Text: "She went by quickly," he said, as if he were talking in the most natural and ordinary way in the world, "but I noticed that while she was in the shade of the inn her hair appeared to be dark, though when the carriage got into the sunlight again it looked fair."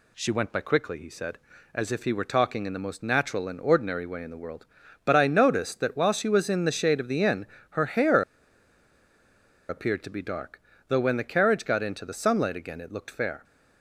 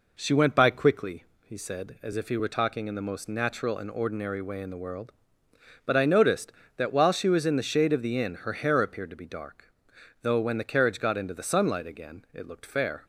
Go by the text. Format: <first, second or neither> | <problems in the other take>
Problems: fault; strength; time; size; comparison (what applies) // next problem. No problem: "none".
second | pauses between "inn" and "her"; slight; at 7.4 s; 0.24 s long // pauses between "hair" and "appeared"; strong; at 8.2 s; 1.4 s long